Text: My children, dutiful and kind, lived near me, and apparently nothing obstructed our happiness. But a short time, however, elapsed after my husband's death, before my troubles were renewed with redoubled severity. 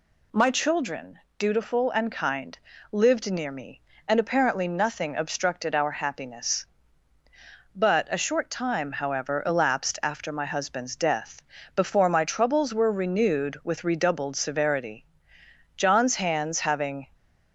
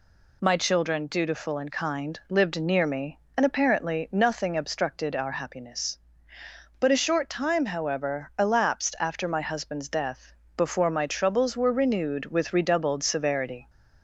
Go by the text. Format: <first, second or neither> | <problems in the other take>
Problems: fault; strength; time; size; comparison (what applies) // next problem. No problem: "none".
second | goes on to say "John's hands having"; from 15.7 s on; 1.3 s long